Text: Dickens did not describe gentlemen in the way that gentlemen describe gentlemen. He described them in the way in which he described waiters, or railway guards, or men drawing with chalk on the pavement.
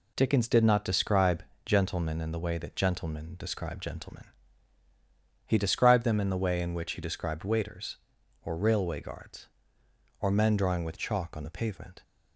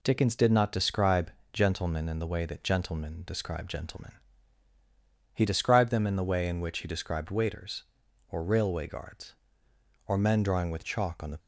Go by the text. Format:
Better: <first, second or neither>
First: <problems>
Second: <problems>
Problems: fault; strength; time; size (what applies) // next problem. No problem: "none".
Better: first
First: pauses between "describe" and "gentlemen"; slight; at 1.4 s; 0.24 s long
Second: pauses between "describe" and "gentlemen"; slight; at 1.2 s; 0.24 s long // stops before "pavement"; at 11.3 s